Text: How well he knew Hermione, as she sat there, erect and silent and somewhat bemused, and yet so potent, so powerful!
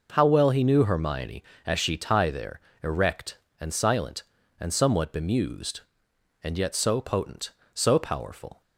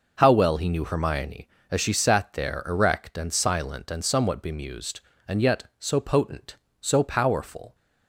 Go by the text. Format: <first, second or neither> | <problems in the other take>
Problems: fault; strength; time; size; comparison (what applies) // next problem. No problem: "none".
second | says "tie" for "sat"; at 1.9 s